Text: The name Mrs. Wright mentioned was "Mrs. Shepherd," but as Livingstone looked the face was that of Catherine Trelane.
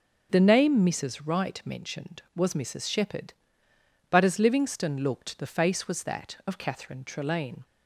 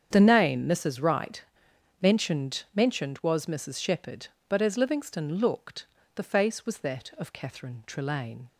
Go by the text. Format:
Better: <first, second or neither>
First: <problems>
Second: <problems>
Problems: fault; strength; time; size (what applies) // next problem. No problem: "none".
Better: first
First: starts louder than the rest; until 1.3 s; 6.5 dB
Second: starts louder than the rest; strong; until 1.1 s; 8 dB // pauses between "Wright" and "mentioned"; noticeable; at 1.4 s; 0.60 s long // says "mentioned" twice; at 2.7 s // pauses between "looked" and "the"; slight; at 5.8 s; 0.30 s long